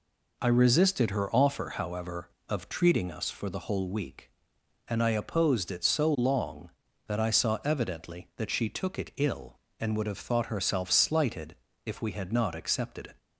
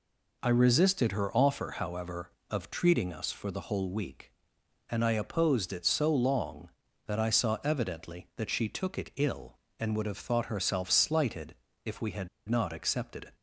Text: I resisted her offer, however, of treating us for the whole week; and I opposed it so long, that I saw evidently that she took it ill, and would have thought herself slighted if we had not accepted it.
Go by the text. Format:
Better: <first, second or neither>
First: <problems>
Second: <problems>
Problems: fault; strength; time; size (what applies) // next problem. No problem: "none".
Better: first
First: pauses between "slighted" and "if"; slight; at 11.5 s; 0.28 s long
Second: pauses between "slighted" and "if"; slight; at 11.5 s; 0.28 s long // pauses between "had" and "not"; slight; at 12.2 s; 0.20 s long